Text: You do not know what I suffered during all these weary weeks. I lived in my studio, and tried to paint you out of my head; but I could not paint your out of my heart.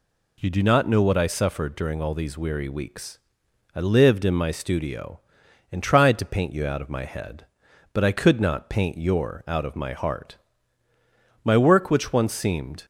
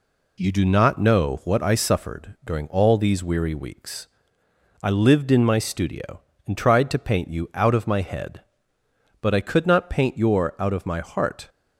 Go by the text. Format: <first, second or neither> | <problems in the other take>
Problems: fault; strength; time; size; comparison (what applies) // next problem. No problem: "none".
second | goes on to say "My work which once seemed"; from 11.4 s on; 1.4 s long